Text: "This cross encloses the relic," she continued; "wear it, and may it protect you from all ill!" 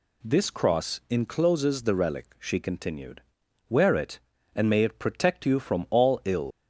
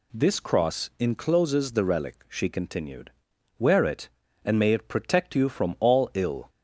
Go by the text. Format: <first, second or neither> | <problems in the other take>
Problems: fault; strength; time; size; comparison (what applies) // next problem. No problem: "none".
second | leaves "ill" unfinished; at 6.5 s; 90 ms